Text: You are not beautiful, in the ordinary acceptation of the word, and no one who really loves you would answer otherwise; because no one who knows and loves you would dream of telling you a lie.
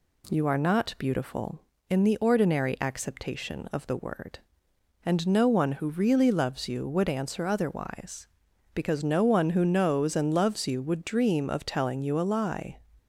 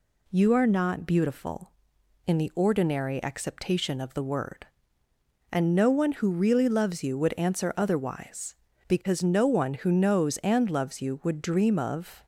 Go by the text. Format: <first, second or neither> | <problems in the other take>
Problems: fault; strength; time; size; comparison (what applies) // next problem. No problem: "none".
first | stops before "telling you a lie"; at 12.2 s